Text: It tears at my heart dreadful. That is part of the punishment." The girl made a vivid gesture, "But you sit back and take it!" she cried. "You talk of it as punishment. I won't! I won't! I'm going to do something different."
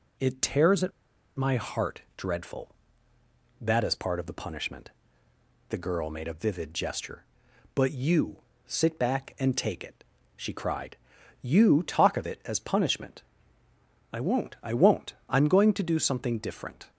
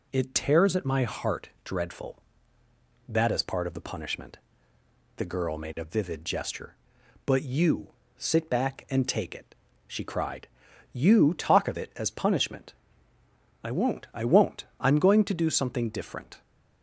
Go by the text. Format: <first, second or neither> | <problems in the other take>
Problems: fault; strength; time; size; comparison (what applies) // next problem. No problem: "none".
second | pauses between "at" and "my"; noticeable; at 0.9 s; 0.47 s long // pauses between "heart" and "dreadful"; slight; at 2.0 s; 0.16 s long; slight in the second // pauses between "you" and "sit"; slight; at 8.4 s; 0.26 s long; slight in the second